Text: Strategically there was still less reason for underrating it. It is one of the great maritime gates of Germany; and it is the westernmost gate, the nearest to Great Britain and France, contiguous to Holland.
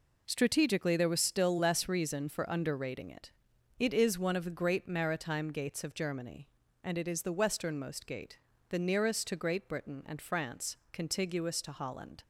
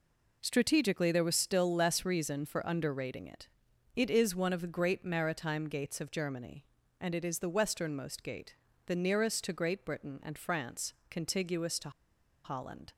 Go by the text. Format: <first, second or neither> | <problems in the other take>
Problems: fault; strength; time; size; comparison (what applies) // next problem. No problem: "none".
first | pauses between "to" and "Holland"; noticeable; at 11.8 s; 0.54 s long